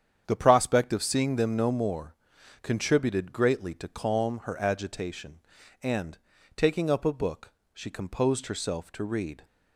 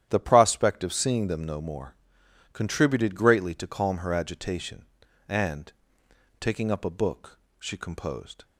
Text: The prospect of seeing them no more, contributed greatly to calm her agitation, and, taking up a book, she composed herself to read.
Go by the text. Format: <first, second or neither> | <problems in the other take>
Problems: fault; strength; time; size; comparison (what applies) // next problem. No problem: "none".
first | starts louder than the rest; strong; until 1.1 s; 10.5 dB; strong in the first // stops before "herself to read"; at 8.4 s